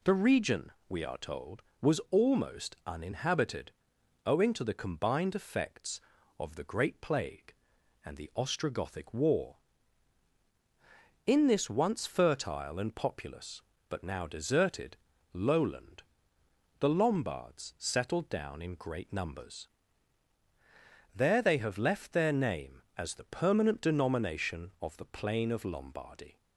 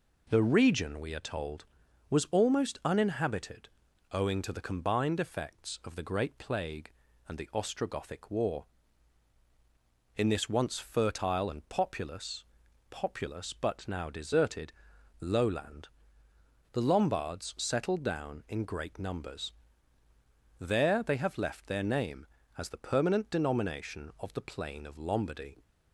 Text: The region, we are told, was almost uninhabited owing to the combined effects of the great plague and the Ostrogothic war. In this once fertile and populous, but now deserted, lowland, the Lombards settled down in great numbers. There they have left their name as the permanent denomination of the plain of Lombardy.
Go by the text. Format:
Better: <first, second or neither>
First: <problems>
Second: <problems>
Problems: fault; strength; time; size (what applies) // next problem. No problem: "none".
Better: first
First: pauses between "uninhabited" and "owing"; noticeable; at 3.7 s; 0.52 s long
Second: pauses between "uninhabited" and "owing"; at 3.6 s; 0.42 s long // says "populous" twice; at 12.8 s